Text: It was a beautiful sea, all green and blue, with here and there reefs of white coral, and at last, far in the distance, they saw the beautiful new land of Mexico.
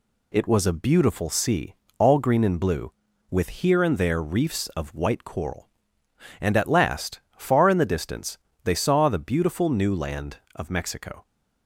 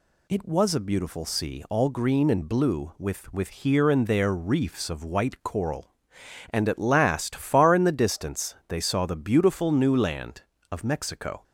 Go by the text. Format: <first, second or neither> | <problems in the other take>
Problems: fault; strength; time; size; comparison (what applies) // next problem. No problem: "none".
first | says "with" twice; at 3.3 s